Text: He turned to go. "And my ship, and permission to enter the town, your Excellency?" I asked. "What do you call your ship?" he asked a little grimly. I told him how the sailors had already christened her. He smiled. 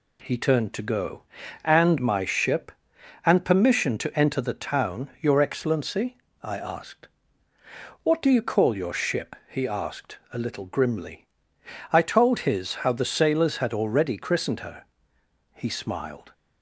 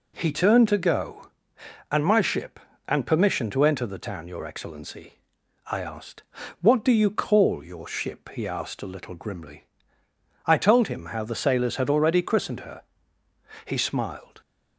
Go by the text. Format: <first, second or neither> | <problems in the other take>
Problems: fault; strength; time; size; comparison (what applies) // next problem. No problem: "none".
second | says "his" for "him"; at 12.4 s